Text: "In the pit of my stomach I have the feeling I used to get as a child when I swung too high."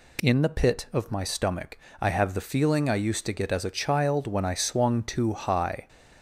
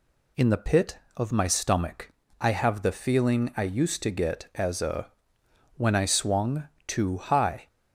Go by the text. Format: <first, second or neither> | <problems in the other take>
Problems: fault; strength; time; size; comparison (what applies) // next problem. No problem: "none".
first | pauses between "stomach" and "I"; slight; at 2.1 s; 0.30 s long; slight in the first // skips "child"; at 5.4 s // pauses between "swung" and "too"; slight; at 6.6 s; 0.20 s long